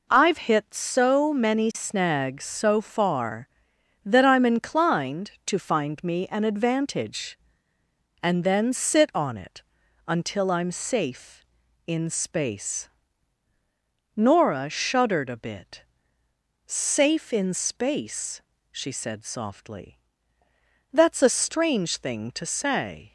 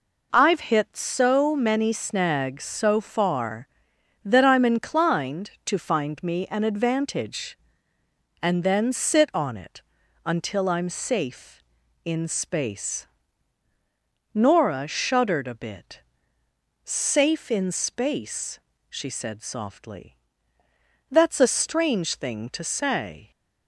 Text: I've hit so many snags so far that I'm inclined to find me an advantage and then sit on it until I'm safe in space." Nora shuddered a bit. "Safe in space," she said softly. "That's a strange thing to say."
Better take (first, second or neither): neither